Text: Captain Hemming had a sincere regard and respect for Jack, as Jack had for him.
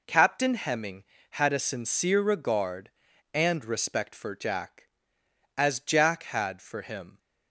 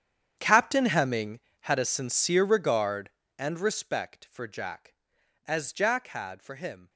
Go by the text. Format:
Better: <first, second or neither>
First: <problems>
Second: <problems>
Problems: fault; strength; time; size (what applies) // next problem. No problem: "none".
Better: first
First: none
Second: gets quieter; strong; throughout; 18 dB